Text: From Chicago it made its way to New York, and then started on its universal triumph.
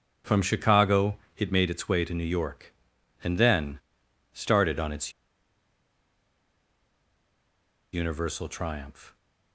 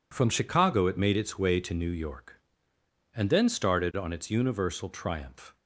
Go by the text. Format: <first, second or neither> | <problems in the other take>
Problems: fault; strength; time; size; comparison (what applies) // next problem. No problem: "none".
second | pauses between "Chicago" and "it"; slight; at 1.1 s; 0.20 s long // pauses between "then" and "started"; noticeable; at 3.7 s; 0.56 s long // pauses between "its" and "universal"; strong; at 5.1 s; 2.8 s long